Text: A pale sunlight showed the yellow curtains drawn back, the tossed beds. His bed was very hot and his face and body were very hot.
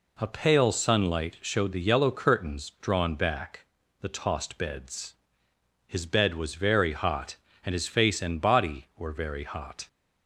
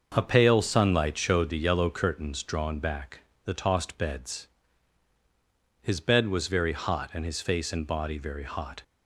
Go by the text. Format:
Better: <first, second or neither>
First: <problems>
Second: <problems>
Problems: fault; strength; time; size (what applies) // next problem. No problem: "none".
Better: first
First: none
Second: starts louder than the rest; until 1.1 s; 6.5 dB // skips "were"; at 8.1 s